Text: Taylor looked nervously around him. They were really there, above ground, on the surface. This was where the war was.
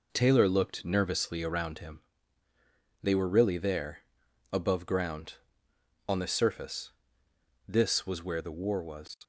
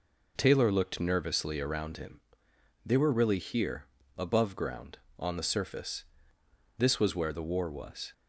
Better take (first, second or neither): first